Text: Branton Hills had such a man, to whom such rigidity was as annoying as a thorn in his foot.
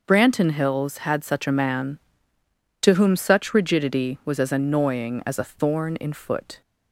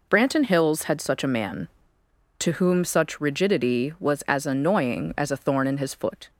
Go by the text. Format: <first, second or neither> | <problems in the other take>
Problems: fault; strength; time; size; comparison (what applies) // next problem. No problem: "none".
second | skips "his"; at 6.1 s